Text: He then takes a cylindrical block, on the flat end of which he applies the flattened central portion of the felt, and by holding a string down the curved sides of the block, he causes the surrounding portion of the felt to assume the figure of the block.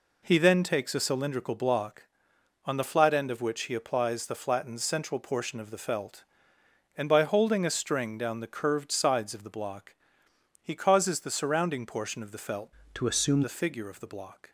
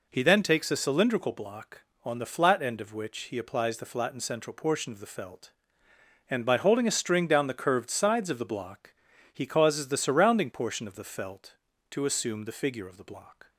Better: second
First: changes voice from "to" to "assume"; from 12.9 to 13.4 s; 0.5 s long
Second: none

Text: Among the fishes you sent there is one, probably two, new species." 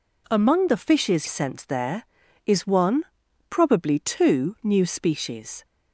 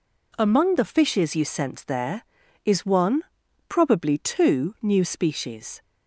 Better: second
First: skips "you"; at 1.2 s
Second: none

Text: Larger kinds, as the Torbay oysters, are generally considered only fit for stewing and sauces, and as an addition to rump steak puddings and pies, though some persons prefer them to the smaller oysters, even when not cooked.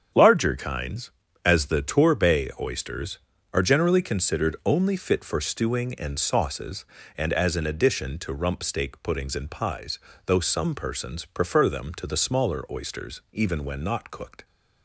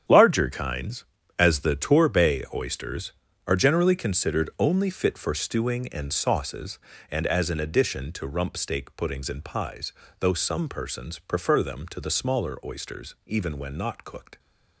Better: first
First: starts louder than the rest; strong; until 1.4 s; 8 dB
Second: gets quieter; strong; throughout; 12 dB // starts louder than the rest; strong; until 1.4 s; 9 dB

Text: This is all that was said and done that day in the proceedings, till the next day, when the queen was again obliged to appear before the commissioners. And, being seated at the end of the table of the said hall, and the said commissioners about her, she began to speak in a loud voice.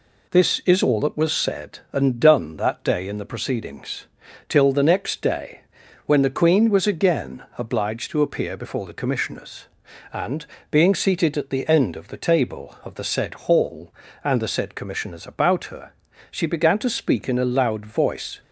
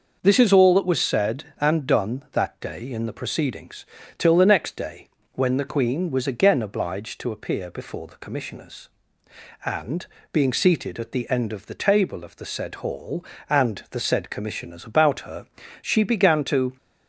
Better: first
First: none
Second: stops before "speak in a loud voice"; at 16.7 s

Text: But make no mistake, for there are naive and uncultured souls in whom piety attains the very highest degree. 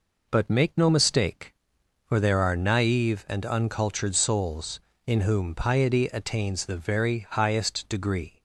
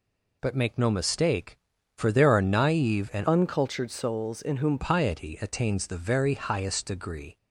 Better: first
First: none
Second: changes voice from "uncultured" to "whom"; from 3.2 to 4.7 s; 1.5 s long

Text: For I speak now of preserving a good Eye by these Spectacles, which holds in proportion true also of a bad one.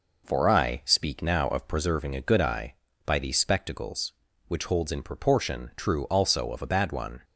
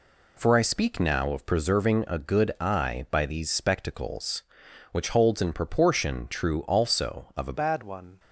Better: first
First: none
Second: changes voice at "bad"; from 7.5 s on; 0.6 s long

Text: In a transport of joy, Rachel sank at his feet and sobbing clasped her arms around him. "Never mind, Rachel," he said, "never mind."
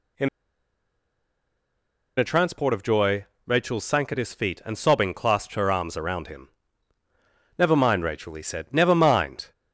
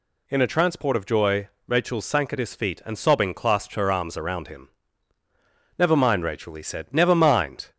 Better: second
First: pauses between "In" and "a"; strong; at 0.2 s; 1.8 s long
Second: none

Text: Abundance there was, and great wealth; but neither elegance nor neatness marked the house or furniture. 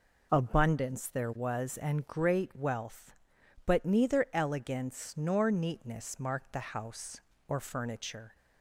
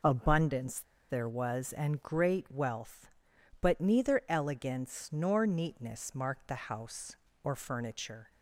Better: first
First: none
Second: pauses between "Abundance" and "there"; slight; at 0.8 s; 0.27 s long

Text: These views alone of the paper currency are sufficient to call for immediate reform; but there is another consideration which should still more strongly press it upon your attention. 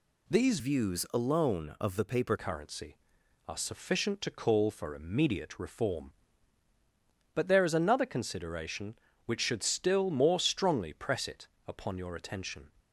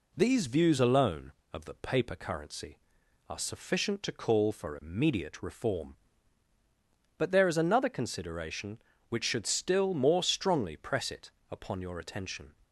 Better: second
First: changes voice from "views" to "paper"; from 0.5 to 2.3 s; 1.8 s long // pauses between "it" and "upon"; slight; at 11.4 s; 0.20 s long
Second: pauses between "it" and "upon"; slight; at 11.3 s; 0.20 s long

